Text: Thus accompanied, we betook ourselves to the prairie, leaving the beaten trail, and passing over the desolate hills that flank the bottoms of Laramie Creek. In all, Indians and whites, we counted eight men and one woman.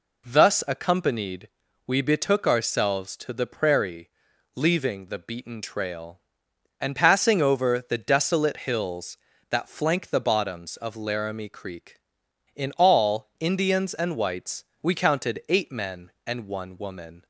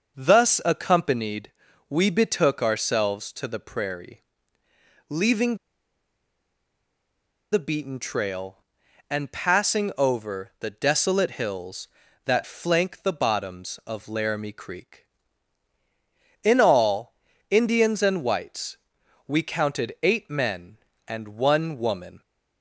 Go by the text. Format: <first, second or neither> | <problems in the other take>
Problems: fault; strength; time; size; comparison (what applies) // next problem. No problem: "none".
first | pauses between "leaving" and "the"; strong; at 5.5 s; 1.9 s long